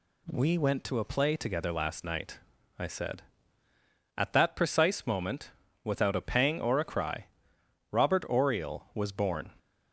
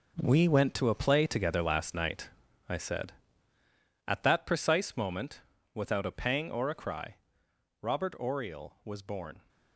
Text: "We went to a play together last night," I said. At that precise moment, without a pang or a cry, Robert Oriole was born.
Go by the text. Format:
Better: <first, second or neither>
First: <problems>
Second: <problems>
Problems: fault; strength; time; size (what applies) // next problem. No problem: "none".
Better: first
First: none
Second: gets quieter; strong; throughout; 10.5 dB